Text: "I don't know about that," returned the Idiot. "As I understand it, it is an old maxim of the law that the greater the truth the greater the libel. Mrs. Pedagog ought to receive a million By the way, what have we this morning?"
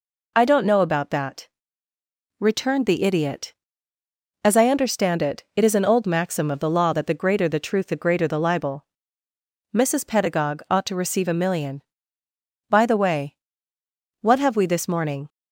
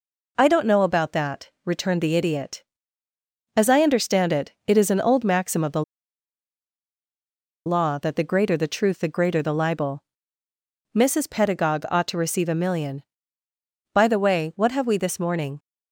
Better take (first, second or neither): first